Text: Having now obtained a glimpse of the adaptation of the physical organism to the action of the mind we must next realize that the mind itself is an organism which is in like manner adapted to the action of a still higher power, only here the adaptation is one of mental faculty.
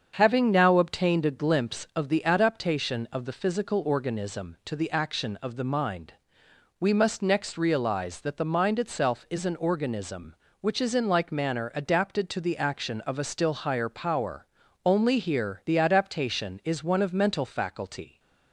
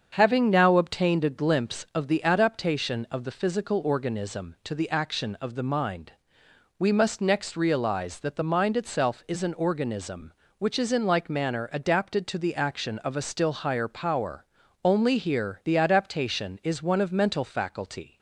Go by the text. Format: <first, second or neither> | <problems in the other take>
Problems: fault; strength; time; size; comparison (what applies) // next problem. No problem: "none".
neither | starts louder than the rest; the same in both // pauses between "mind" and "we"; noticeable; the same in both